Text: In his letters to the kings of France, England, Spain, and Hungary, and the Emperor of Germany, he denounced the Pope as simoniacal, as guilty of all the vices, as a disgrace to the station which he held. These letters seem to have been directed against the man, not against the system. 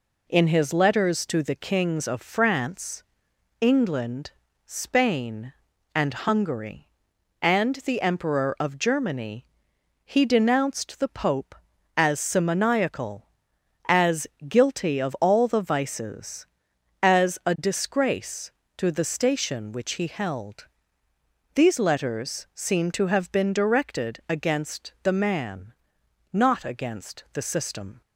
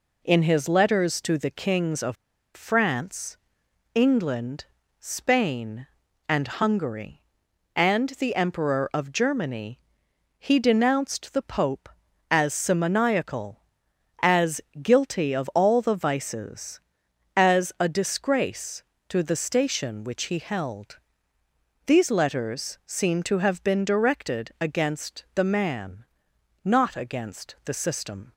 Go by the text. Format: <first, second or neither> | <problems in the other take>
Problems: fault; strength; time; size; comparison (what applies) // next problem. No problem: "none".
first | pauses between "of" and "France"; at 2.1 s; 0.39 s long // pauses between "as" and "guilty"; slight; at 14.6 s; 0.22 s long; slight in the first